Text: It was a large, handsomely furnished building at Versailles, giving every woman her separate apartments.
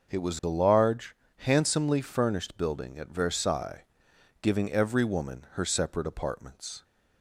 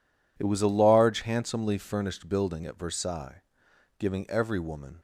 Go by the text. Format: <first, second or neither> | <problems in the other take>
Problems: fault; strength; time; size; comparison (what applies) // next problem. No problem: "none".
first | stops before "her separate apartments"; at 4.9 s